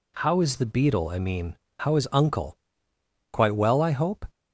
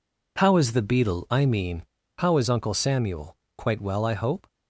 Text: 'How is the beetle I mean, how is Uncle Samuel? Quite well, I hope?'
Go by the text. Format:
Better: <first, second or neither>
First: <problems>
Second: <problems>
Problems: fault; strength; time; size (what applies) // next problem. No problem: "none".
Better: second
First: skips "Samuel"; at 2.9 s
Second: none